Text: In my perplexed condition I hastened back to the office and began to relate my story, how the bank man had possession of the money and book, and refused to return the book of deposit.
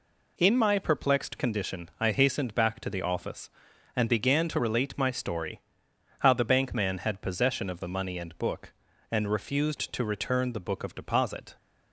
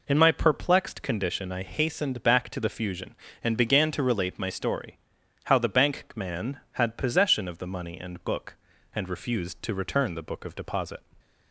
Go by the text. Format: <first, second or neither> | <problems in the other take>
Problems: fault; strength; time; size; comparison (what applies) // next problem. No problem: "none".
first | says "fusion" for "office"; at 2.6 s